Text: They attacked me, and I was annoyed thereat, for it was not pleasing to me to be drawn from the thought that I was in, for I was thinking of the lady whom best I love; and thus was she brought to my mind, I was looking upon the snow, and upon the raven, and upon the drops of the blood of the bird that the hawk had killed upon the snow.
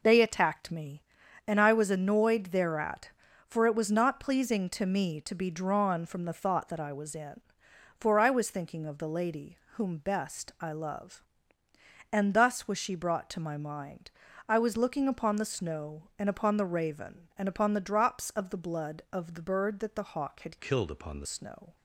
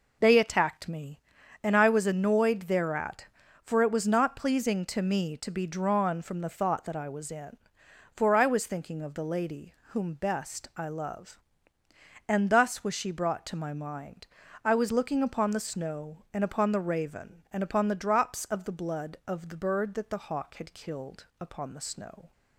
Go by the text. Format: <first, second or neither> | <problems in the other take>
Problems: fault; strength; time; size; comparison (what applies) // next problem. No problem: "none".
second | pauses between "lady" and "whom"; slight; at 9.5 s; 0.18 s long; slight in the second // changes voice from "killed" to "the"; from 20.5 to 21.2 s; 0.7 s long